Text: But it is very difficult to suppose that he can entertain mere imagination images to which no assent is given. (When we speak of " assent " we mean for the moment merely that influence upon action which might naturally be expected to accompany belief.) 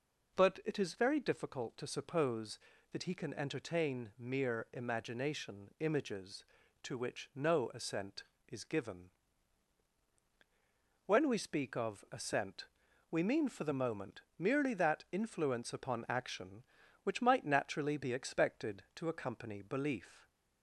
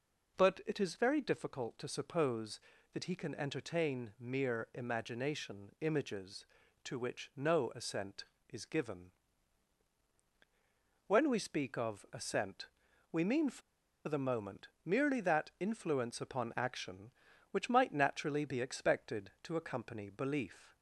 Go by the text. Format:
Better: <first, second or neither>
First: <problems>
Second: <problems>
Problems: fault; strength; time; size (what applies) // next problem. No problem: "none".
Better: first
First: pauses between "moment" and "merely"; slight; at 14.2 s; 0.16 s long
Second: pauses between "for" and "the"; noticeable; at 13.6 s; 0.46 s long // pauses between "moment" and "merely"; slight; at 14.6 s; 0.16 s long